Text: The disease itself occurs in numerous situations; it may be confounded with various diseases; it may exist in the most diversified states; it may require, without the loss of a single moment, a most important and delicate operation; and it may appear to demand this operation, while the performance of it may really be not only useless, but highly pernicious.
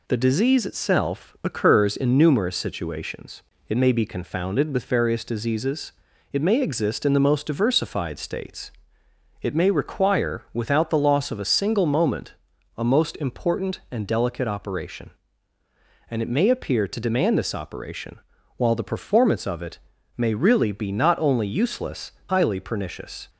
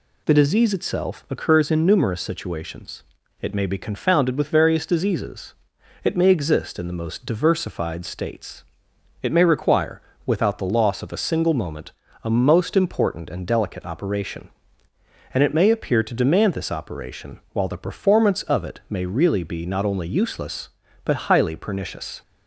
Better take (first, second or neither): second